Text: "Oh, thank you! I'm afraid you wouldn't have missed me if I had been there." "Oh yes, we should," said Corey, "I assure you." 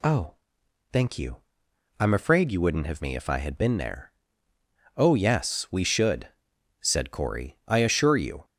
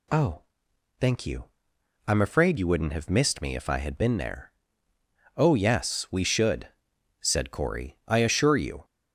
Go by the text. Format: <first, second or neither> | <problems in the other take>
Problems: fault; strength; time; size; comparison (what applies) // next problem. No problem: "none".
second | skips "missed"; at 3.0 s